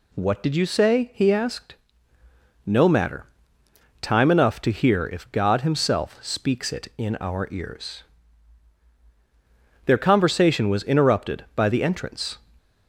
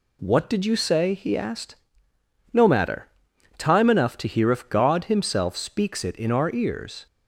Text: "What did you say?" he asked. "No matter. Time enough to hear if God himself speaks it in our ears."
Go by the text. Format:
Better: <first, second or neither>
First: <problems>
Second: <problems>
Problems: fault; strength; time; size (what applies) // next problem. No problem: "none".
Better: second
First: goes on to say "Their conversation was interrupted by the entrance"; strong; from 9.8 s on; 2.5 s long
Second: none